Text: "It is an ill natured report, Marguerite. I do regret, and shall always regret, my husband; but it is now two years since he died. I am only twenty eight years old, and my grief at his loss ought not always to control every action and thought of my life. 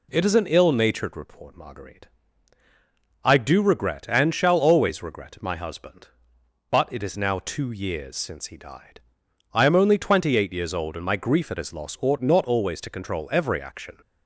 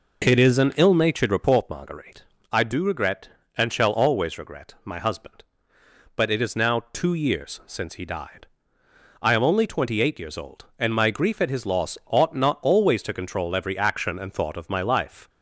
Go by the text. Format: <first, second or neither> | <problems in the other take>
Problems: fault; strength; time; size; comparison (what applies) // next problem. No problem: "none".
second | stops before "and thought of my life"; at 14.0 s